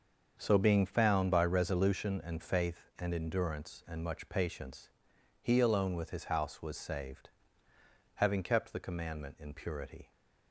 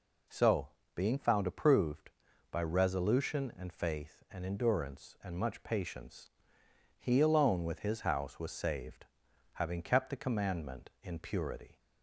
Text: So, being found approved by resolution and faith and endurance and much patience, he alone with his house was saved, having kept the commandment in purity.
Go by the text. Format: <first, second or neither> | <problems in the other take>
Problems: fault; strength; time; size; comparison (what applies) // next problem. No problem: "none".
second | starts louder than the rest; until 1.3 s; 6.5 dB // skips "approved"; at 1.3 s